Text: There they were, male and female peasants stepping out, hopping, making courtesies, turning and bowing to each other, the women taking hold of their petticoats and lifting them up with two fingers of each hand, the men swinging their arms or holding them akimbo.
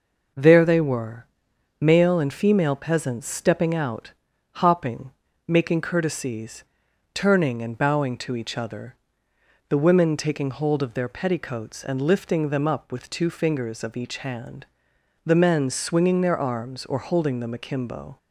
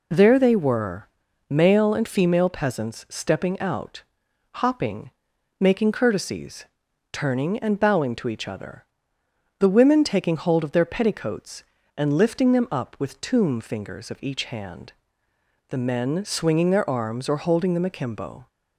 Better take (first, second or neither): first